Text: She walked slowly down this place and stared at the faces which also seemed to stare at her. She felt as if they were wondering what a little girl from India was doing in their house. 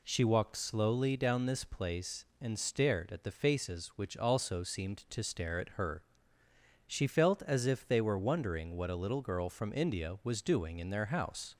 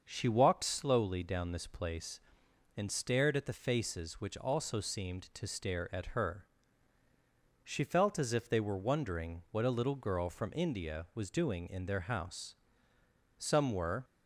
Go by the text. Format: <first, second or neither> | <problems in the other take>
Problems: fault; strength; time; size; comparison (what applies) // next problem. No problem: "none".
first | starts louder than the rest; until 1.0 s; 6.5 dB // goes on to say "Some were"; noticeable; from 13.3 s on; 0.66 s long